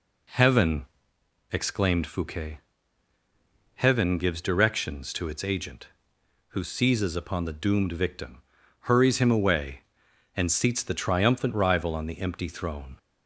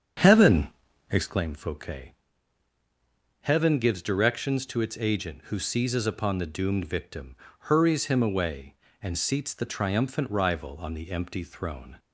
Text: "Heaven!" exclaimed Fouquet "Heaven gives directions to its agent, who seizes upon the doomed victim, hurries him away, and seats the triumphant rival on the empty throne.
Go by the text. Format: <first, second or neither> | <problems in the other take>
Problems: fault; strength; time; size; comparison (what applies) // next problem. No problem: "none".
first | starts louder than the rest; strong; until 1.4 s; 7.5 dB // pauses between "Fouquet" and "Heaven"; strong; at 2.1 s; 1.2 s long; also in the first